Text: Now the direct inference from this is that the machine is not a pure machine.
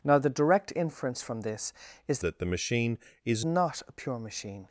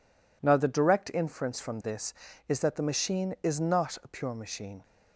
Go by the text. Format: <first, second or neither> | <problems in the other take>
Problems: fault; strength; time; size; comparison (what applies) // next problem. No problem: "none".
second | changes voice from "that" to "is"; from 2.2 to 3.4 s; 1.2 s long